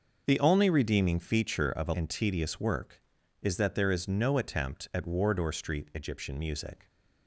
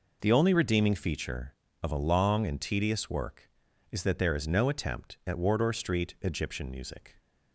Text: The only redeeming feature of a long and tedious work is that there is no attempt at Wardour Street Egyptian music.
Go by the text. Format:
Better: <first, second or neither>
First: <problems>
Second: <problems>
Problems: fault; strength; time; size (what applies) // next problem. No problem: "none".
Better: second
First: starts louder than the rest; noticeable; until 1.2 s; 6 dB // skips "long"; at 1.9 s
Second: none